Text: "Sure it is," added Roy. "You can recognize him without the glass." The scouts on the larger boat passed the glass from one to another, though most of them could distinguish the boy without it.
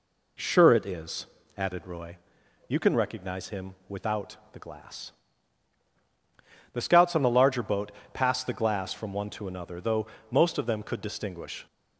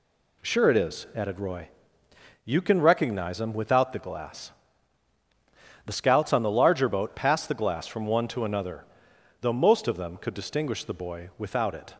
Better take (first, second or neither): second